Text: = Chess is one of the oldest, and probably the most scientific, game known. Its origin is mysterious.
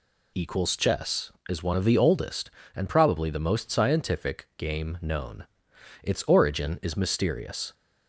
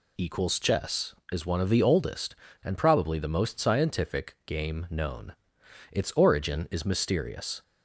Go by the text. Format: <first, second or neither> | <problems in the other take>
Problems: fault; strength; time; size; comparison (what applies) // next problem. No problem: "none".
neither | none